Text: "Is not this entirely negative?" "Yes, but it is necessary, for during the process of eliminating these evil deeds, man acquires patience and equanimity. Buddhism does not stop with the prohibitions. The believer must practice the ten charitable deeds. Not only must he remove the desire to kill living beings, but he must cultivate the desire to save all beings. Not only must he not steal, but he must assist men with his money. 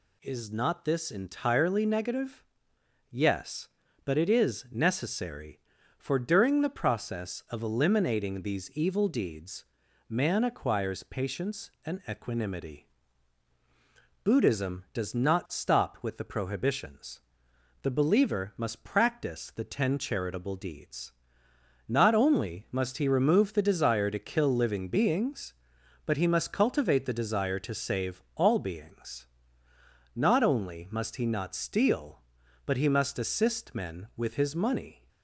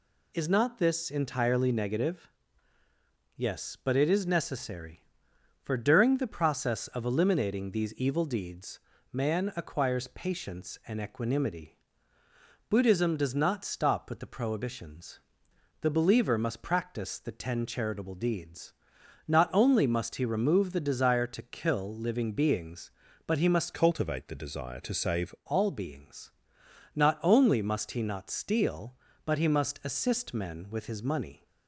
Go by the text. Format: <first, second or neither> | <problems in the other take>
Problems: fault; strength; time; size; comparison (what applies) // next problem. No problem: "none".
first | changes voice from "cultivate" to "save"; from 23.7 to 25.3 s; 1.6 s long